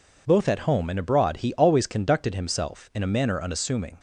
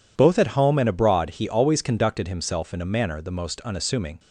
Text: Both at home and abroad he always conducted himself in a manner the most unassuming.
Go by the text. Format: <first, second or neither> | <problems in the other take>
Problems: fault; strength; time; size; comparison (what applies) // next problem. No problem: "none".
second | skips "the most"; at 3.3 s